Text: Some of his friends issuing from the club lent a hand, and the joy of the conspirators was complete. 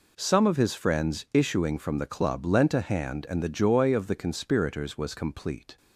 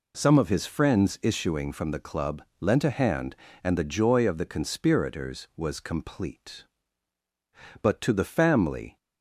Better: first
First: none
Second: pauses between "club" and "lent"; slight; at 2.4 s; 0.20 s long // goes on to say "But to the family"; noticeable; from 7.8 s on; 1.1 s long

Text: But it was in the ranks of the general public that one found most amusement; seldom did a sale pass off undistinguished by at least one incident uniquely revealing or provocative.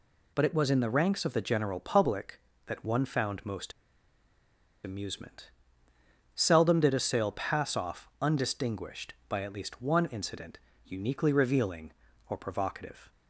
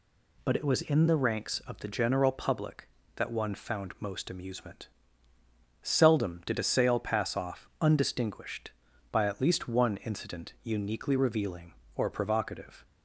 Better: second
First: pauses between "most" and "amusement"; at 3.7 s; 1.1 s long // pauses between "incident" and "uniquely"; slight; at 10.5 s; 0.30 s long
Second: none

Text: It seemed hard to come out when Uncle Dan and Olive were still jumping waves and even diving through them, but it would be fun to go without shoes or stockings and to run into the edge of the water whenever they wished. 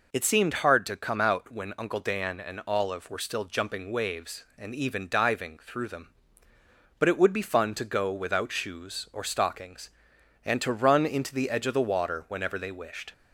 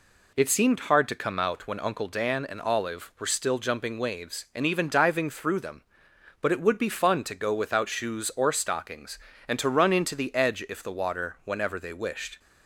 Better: first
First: none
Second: says "if" for "of"; at 10.6 s

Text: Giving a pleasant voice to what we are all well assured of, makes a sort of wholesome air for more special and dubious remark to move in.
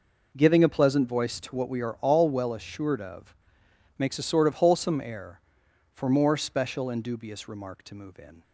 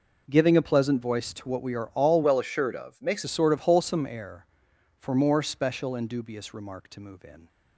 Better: first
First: none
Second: changes voice from "well" to "makes"; from 2.2 to 3.2 s; 1.0 s long

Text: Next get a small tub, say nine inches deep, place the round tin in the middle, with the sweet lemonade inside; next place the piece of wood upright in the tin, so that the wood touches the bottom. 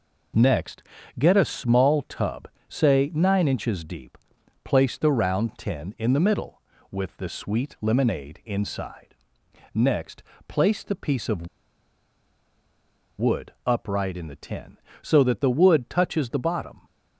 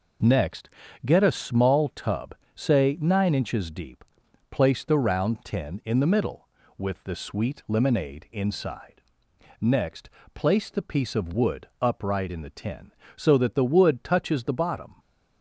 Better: second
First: pauses between "Next" and "get"; slight; at 0.8 s; 0.34 s long // pauses between "next" and "place"; slight; at 10.2 s; 0.24 s long // pauses between "of" and "wood"; strong; at 11.4 s; 1.7 s long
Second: pauses between "Next" and "get"; slight; at 0.6 s; 0.34 s long // pauses between "next" and "place"; slight; at 10.1 s; 0.24 s long

